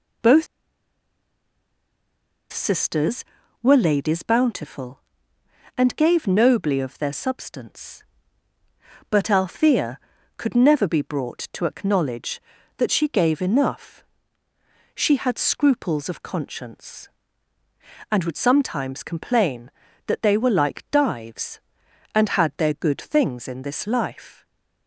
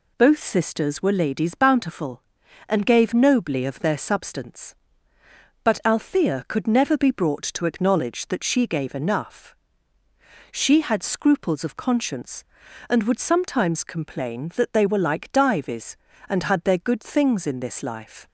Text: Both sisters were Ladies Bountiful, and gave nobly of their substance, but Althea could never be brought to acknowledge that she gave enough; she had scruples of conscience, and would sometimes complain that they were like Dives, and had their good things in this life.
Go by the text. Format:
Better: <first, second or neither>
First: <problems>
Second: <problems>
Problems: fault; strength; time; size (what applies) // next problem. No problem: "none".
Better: second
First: pauses between "Both" and "sisters"; strong; at 0.4 s; 2.0 s long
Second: none